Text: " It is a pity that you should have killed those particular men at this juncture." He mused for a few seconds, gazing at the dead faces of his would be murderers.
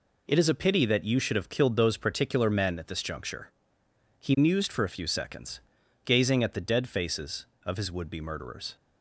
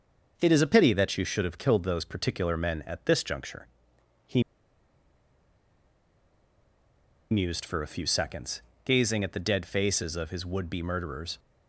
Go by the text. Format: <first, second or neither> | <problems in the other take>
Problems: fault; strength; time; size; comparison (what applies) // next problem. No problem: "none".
first | starts louder than the rest; until 1.3 s; 6.5 dB // pauses between "He" and "mused"; strong; at 4.4 s; 2.8 s long